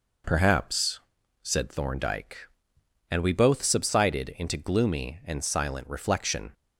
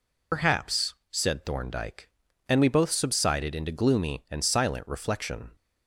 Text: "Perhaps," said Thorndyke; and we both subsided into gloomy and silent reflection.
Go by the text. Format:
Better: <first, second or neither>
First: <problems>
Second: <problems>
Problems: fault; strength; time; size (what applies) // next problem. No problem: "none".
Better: first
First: none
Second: loses the start of "Perhaps"; at 0.3 s; 90 ms